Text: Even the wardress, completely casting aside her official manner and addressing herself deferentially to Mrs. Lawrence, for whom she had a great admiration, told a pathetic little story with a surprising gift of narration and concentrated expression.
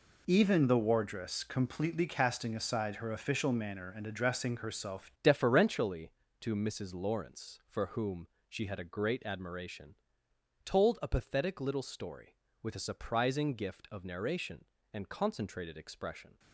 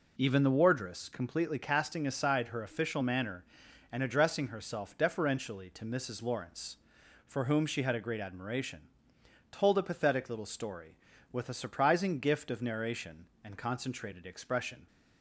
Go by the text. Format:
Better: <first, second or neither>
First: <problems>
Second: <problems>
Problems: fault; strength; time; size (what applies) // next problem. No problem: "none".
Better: second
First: changes voice at "deferentially"; from 5.2 s on; 11.1 s long // pauses between "whom" and "she"; slight; at 8.2 s; 0.22 s long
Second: none